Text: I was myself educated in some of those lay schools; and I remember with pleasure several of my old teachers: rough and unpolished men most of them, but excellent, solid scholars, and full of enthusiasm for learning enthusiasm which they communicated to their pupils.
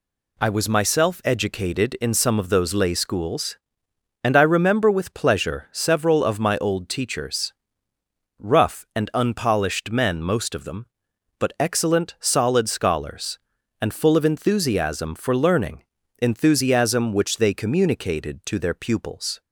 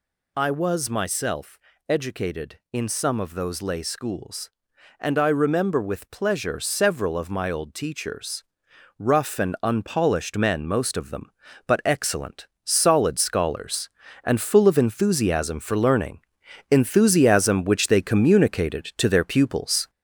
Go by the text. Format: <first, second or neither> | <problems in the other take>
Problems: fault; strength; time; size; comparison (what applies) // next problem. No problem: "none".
first | gets louder; noticeable; throughout; 4 dB // pauses between "myself" and "educated"; slight; at 1.5 s; 0.30 s long // pauses between "learning" and "enthusiasm"; noticeable; at 16.2 s; 0.48 s long; slight in the first